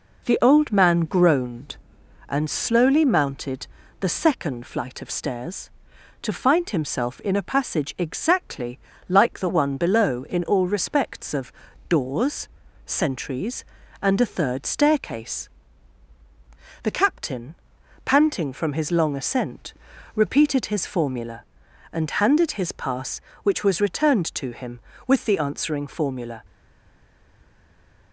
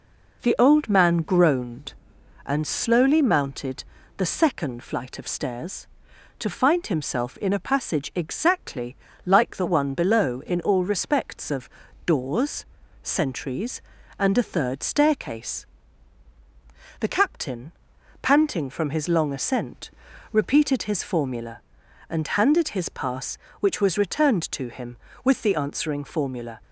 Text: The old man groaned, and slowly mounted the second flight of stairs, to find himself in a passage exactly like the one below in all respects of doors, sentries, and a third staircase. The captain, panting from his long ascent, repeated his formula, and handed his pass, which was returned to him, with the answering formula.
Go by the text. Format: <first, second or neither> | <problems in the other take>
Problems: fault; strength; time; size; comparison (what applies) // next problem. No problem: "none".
second | pauses between "mounted" and "the"; slight; at 3.6 s; 0.32 s long; slight in the second // pauses between "exactly" and "like"; slight; at 8.7 s; 0.30 s long; slight in the second // pauses between "of" and "doors"; at 11.5 s; 0.38 s long; also in the second // stays silent after the last word; noticeable; from 26.4 s on; 1.7 s long